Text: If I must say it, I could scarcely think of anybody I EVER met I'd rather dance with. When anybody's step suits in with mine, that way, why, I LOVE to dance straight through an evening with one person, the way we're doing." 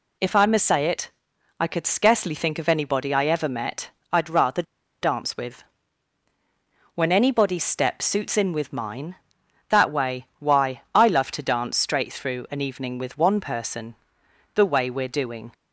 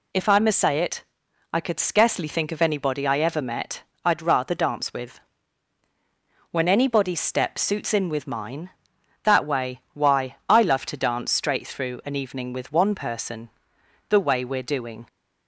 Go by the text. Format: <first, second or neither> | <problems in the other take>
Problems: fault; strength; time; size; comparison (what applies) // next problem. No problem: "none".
second | pauses between "met" and "I'd"; slight; at 3.9 s; 0.20 s long; slight in the second // pauses between "rather" and "dance"; at 4.6 s; 0.39 s long